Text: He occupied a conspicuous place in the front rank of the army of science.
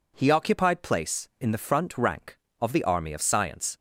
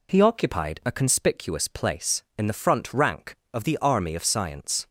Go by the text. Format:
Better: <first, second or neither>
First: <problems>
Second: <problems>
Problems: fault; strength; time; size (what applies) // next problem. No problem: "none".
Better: second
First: skips "a conspicuous"; at 0.8 s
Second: none